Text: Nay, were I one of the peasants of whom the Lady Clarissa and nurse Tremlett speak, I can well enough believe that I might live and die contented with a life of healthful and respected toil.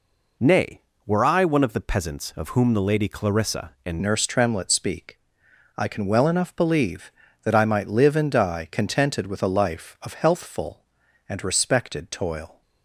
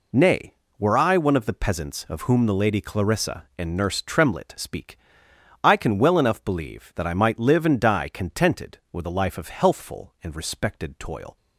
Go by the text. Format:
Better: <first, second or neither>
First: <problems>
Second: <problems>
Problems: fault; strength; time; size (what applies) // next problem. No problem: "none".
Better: second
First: changes voice at "nurse"; from 3.9 s on; 8.7 s long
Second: none